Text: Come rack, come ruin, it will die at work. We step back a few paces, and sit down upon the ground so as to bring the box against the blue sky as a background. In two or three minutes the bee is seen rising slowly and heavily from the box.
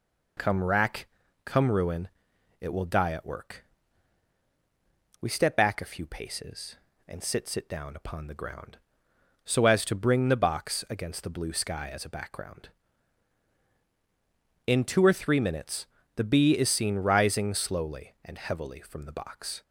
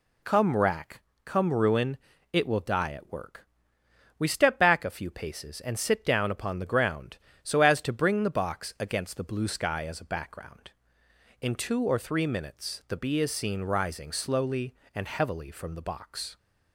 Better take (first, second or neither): second